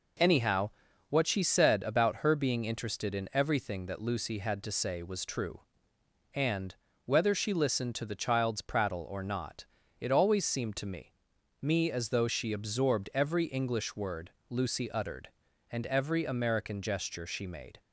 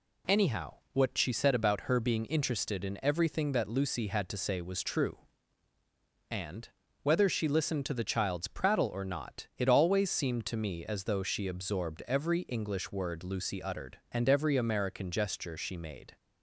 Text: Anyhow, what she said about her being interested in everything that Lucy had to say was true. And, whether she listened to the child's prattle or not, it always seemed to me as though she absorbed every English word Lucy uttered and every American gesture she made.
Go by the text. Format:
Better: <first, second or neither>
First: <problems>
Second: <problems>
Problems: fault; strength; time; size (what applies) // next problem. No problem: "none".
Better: second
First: says "me" twice; at 11.5 s // pauses between "word" and "Lucy"; slight; at 14.2 s; 0.18 s long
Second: none